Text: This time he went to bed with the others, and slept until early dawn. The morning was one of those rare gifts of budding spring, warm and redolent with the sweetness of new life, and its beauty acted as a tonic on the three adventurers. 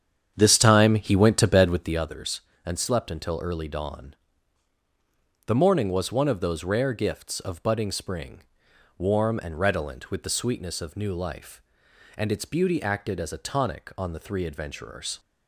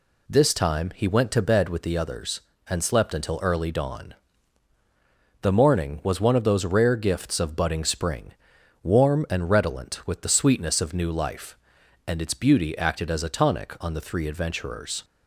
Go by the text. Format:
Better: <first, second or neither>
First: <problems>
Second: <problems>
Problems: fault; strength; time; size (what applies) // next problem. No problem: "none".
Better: second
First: starts louder than the rest; strong; until 2.1 s; 8.5 dB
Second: none